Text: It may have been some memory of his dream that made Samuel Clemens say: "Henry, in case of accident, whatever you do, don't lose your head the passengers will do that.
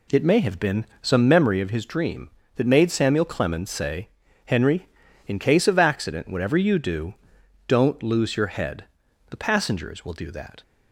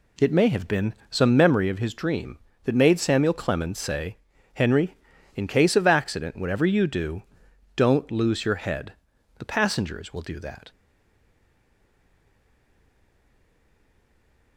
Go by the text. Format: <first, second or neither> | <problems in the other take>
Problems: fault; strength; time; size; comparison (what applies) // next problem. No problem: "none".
first | pauses between "been" and "some"; slight; at 0.9 s; 0.16 s long; slight in the first // pauses between "head" and "the"; at 8.9 s; 0.42 s long; also in the first // stays silent after the last word; strong; from 10.7 s on; 3.8 s long